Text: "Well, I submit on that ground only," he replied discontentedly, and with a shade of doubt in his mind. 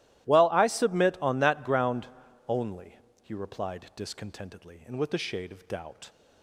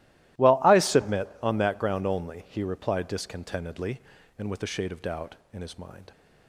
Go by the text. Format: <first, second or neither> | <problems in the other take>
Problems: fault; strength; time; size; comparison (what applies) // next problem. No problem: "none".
second | starts louder than the rest; strong; until 1.3 s; 14.5 dB; strong in the second // pauses between "ground" and "only"; at 2.0 s; 0.40 s long // stops before "in his mind"; at 6.0 s